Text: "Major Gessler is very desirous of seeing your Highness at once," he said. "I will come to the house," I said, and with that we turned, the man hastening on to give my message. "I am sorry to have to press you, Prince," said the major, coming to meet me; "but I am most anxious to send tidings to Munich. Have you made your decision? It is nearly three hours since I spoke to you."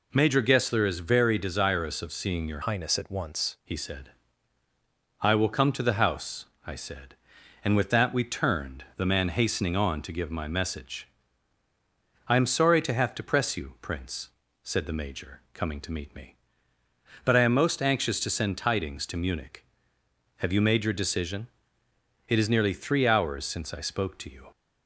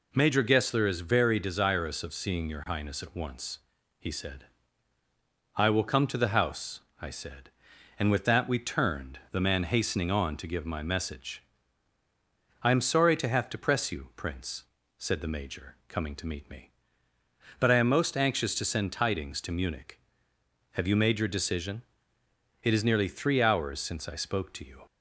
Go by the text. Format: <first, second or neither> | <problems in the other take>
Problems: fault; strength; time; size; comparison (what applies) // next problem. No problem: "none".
second | changes voice from "Highness" to "once"; from 2.6 to 3.5 s; 0.9 s long